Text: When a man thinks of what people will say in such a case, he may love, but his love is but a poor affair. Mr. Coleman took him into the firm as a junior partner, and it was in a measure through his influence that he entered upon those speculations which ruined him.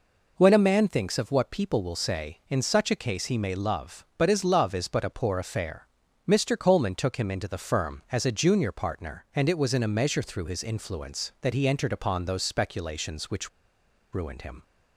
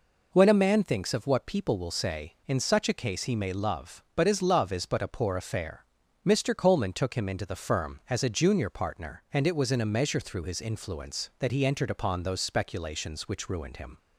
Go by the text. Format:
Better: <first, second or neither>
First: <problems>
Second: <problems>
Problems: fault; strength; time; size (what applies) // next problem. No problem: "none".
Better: second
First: pauses between "which" and "ruined"; noticeable; at 13.4 s; 0.63 s long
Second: none